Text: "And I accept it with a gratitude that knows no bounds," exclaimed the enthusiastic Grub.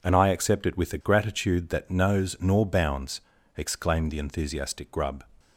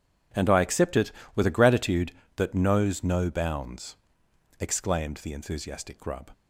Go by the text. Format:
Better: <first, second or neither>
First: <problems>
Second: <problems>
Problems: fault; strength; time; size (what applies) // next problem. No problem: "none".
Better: second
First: says "nor" for "no"; at 2.3 s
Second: none